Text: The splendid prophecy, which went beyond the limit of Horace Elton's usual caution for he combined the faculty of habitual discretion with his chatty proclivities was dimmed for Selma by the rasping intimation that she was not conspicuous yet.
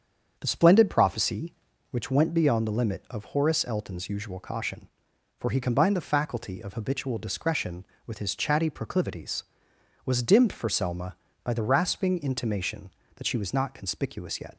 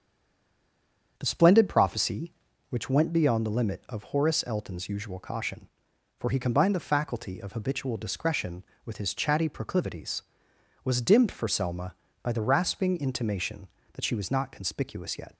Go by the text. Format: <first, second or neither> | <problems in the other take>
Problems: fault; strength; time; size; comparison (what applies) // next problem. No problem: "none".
first | stays silent before the first word; noticeable; until 1.1 s; 1.1 s long // starts louder than the rest; strong; until 2.1 s; 7.5 dB; strong in the first